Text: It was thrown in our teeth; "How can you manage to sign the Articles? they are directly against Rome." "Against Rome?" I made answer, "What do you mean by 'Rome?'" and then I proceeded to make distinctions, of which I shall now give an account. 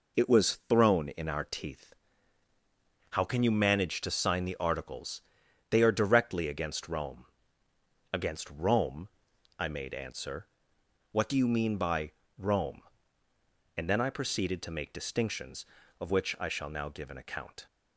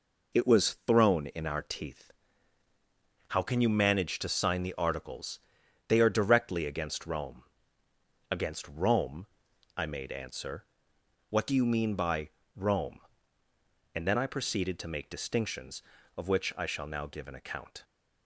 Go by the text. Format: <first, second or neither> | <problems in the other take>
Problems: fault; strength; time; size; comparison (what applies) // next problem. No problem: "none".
neither | pauses between "by" and "Rome"; slight; the same in both